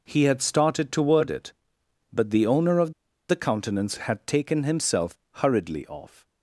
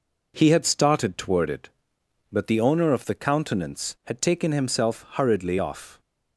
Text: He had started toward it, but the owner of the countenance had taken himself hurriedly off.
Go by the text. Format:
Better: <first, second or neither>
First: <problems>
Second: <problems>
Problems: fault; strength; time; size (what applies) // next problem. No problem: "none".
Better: second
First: pauses between "of" and "the"; at 2.9 s; 0.37 s long // pauses between "himself" and "hurriedly"; slight; at 5.1 s; 0.18 s long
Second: none